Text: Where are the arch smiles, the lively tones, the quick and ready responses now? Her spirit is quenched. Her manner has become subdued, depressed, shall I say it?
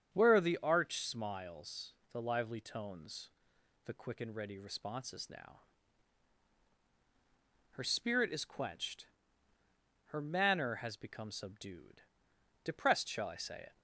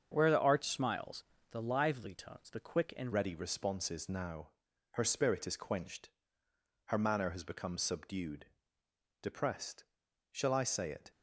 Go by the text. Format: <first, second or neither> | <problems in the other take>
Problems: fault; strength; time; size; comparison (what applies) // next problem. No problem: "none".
first | starts louder than the rest; until 1.1 s; 7 dB; strong in the first // changes voice at "ready"; from 3.1 s on; 8.0 s long